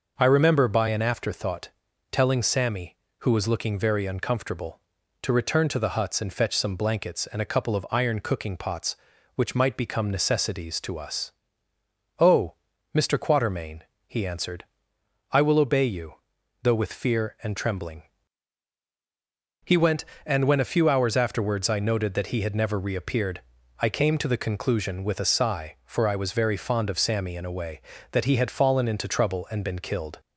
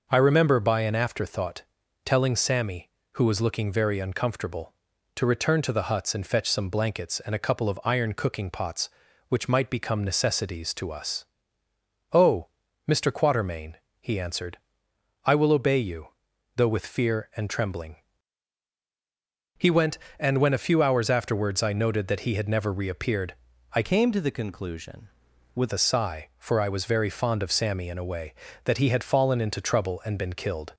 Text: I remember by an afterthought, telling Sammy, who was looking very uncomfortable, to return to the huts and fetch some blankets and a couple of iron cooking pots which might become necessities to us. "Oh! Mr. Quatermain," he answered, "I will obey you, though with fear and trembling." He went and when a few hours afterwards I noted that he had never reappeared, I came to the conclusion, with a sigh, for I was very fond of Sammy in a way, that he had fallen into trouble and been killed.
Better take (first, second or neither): first